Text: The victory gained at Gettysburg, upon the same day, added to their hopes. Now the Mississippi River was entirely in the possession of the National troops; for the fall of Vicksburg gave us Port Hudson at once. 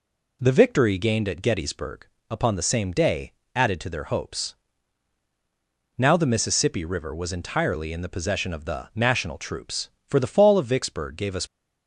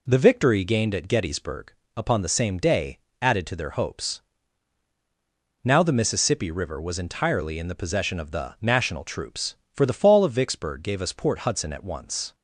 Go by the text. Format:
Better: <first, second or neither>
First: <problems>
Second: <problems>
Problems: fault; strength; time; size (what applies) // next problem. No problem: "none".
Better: second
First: stops before "Port Hudson at once"; at 11.4 s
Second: none